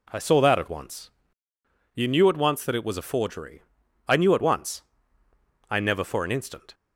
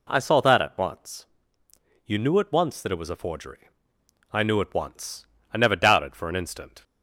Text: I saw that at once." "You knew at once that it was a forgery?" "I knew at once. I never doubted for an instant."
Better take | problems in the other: second | skips "doubted"; at 6.0 s

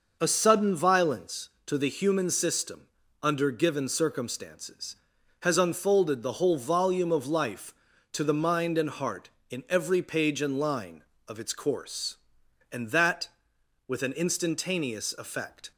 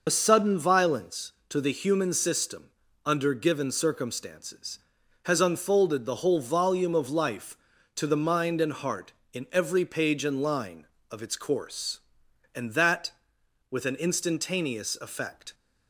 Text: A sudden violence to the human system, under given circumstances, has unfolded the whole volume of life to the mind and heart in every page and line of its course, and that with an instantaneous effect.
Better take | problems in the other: first | loses the start of "A"; at 0.0 s; 40 ms

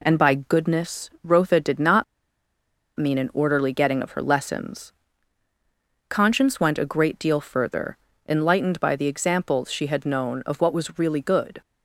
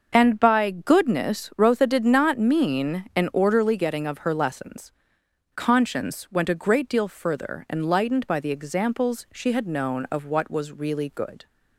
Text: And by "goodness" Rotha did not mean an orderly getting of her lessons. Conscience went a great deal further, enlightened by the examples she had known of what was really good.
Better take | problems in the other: second | pauses between "not" and "mean"; noticeable; at 2.0 s; 0.94 s long

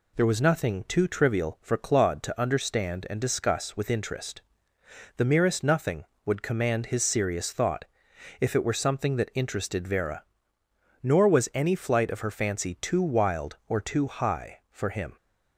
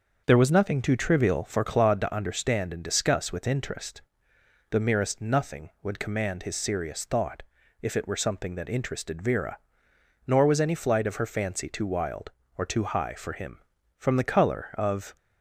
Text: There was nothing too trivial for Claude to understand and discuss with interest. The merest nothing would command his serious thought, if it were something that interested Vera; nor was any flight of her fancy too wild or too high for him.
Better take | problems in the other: first | starts louder than the rest; until 1.2 s; 6.5 dB // goes on to say "From the colour of"; noticeable; from 13.9 s on; 1.1 s long

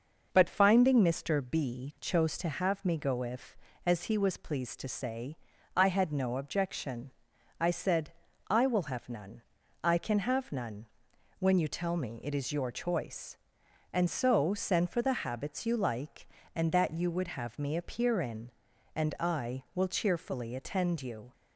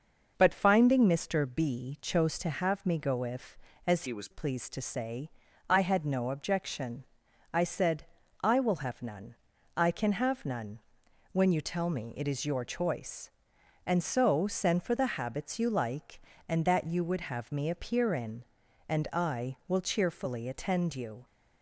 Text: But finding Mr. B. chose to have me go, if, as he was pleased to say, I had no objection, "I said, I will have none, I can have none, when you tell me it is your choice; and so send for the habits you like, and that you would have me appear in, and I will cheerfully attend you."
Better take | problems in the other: first | changes voice from "he" to "was"; from 4.0 to 4.2 s; 0.2 s long

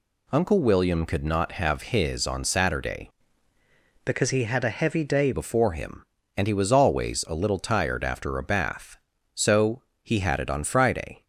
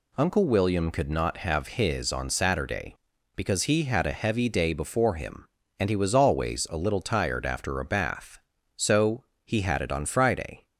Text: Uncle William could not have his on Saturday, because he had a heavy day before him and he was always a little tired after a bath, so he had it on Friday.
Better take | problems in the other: second | changes voice from "because" to "day"; from 4.0 to 5.3 s; 1.3 s long // pauses between "so" and "he"; slight; at 9.8 s; 0.22 s long; slight in the second

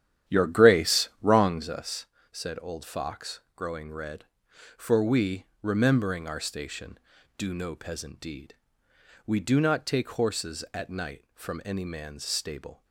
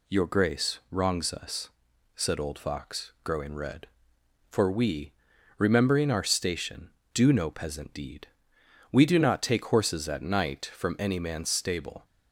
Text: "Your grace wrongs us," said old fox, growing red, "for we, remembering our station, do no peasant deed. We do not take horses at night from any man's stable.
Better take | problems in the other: second | starts louder than the rest; strong; until 1.8 s; 10.5 dB

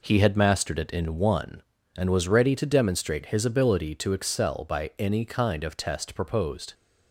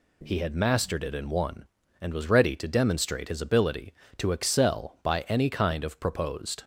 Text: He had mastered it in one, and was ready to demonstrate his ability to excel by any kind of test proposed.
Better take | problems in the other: first | skips "test"; at 5.9 s

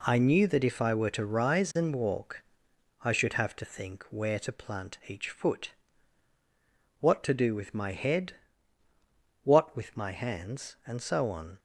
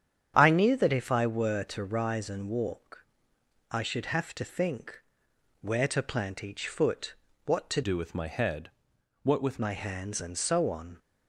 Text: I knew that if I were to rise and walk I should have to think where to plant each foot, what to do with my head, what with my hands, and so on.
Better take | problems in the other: first | starts louder than the rest; strong; until 1.3 s; 9 dB // pauses between "walk" and "I"; noticeable; at 3.0 s; 0.66 s long; noticeable in the first // pauses between "think" and "where"; noticeable; at 4.9 s; 0.62 s long // changes voice from "do" to "with"; from 7.8 to 9.5 s; 1.7 s long

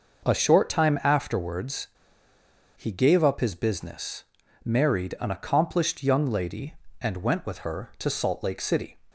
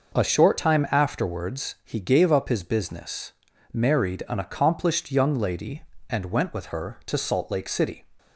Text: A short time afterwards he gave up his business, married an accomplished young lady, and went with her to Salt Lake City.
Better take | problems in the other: second | pauses between "afterwards" and "he"; noticeable; at 1.8 s; 0.89 s long

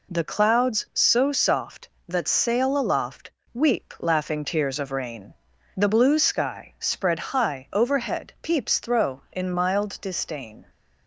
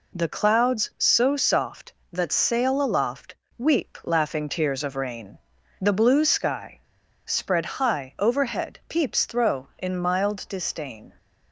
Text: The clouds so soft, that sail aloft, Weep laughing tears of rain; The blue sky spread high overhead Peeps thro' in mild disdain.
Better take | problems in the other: first | pauses between "sky" and "spread"; at 6.8 s; 0.44 s long

